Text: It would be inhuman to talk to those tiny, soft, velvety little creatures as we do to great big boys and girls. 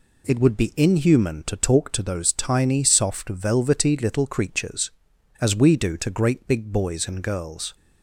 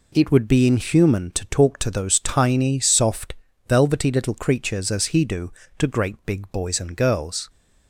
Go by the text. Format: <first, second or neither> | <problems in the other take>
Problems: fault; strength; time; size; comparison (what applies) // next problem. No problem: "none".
first | says "he" for "we"; at 5.0 s